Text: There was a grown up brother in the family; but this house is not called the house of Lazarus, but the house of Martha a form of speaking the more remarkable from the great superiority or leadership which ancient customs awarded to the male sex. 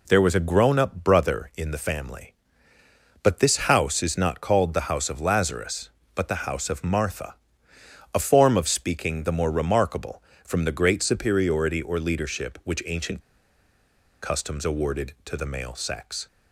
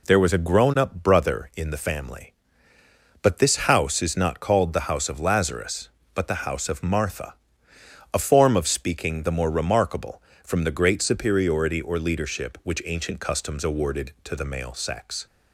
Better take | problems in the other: second | pauses between "Martha" and "a"; noticeable; at 7.3 s; 0.80 s long; noticeable in the second // pauses between "ancient" and "customs"; at 13.2 s; 1.0 s long

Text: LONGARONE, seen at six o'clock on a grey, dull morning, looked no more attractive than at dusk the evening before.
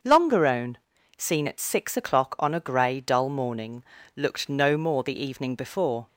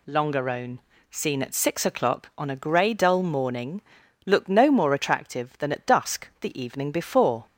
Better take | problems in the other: second | starts louder than the rest; until 1.4 s; 6.5 dB // skips "attractive than at dusk"; at 5.0 s

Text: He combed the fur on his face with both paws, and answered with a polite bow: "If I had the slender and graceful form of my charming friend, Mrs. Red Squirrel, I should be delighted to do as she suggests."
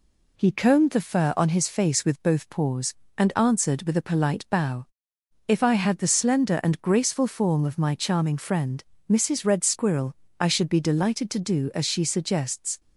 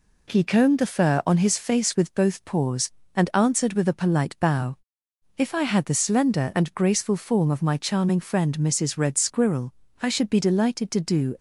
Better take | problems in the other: first | stops before "as she suggests"; at 11.3 s

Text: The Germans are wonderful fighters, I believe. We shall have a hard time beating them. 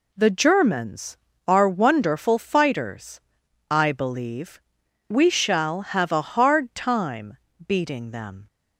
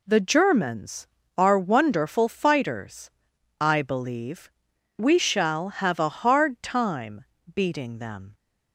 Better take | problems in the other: neither | pauses between "time" and "beating"; slight; the same in both

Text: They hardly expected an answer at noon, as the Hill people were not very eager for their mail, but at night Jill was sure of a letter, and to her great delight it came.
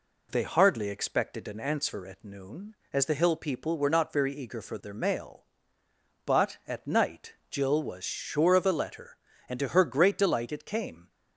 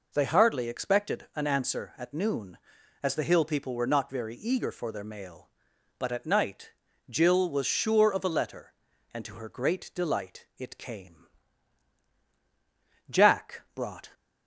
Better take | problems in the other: first | pauses between "night" and "Jill"; slight; at 6.7 s; 0.36 s long; slight in the first // goes on to say "Jack brought"; noticeable; from 13.0 s on; 1.0 s long

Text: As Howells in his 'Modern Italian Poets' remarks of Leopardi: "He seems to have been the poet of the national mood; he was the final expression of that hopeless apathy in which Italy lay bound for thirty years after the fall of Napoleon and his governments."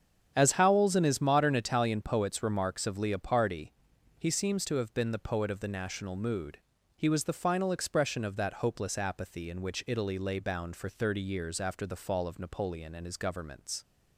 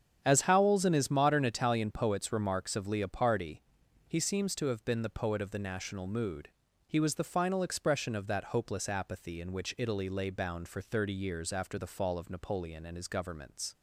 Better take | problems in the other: neither | starts louder than the rest; strong; the same in both

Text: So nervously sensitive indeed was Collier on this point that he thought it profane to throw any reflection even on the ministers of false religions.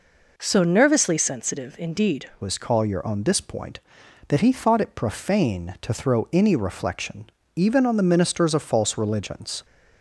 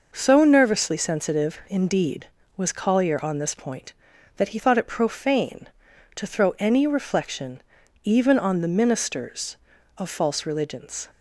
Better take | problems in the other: second | changes voice at "was"; from 2.4 s on; 7.2 s long // pauses between "reflection" and "even"; slight; at 7.2 s; 0.32 s long; also in the second

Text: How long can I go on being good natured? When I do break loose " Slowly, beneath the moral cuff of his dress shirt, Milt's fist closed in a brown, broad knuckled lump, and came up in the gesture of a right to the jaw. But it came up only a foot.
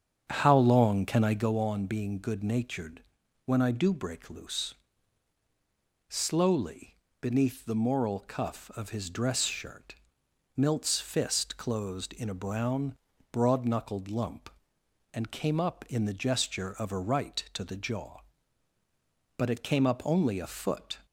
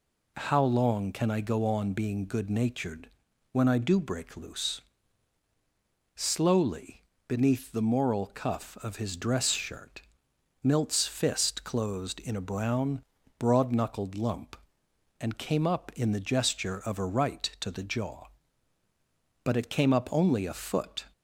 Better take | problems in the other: second | starts louder than the rest; strong; until 1.6 s; 8.5 dB

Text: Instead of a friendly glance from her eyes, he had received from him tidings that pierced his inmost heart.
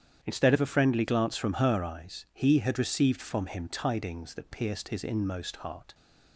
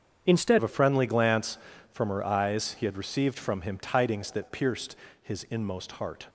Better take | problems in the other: first | starts louder than the rest; strong; until 1.2 s; 7.5 dB; strong in the first // changes voice at "of"; from 0.5 s on; 5.7 s long // pauses between "pierced" and "his"; slight; at 4.9 s; 0.28 s long

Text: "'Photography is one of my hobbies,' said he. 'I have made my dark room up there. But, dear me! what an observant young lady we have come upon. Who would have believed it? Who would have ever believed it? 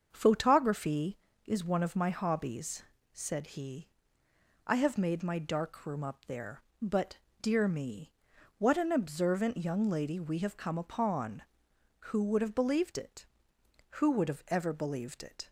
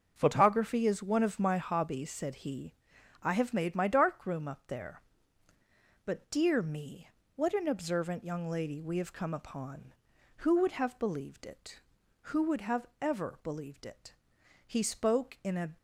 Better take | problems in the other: first | starts louder than the rest; until 1.1 s; 6.5 dB; also in the first // goes on to say "He spoke in a"; noticeable; from 14.6 s on; 1.1 s long

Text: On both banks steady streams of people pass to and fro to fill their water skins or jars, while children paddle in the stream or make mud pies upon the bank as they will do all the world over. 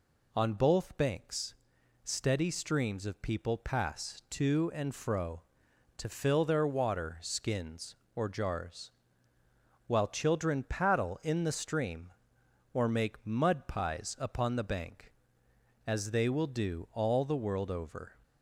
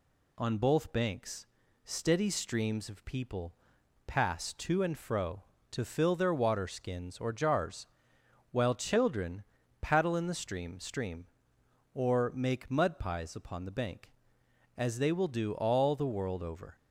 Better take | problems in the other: first | pauses between "banks" and "steady"; at 1.4 s; 0.40 s long; noticeable in the first // pauses between "people" and "pass"; noticeable; at 3.5 s; 0.54 s long // pauses between "children" and "paddle"; at 9.4 s; 0.38 s long // says "stream" twice; at 10.7 s

